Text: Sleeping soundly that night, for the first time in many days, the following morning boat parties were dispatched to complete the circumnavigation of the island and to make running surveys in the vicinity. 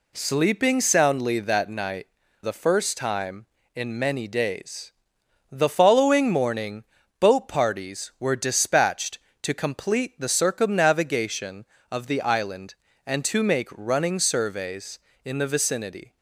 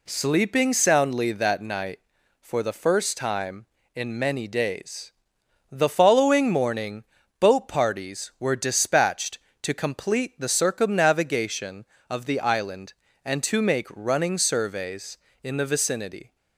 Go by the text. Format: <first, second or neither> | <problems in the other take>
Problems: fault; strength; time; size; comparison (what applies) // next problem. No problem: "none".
second | skips "for"; at 2.2 s // pauses between "morning" and "boat"; at 6.8 s; 0.38 s long; also in the second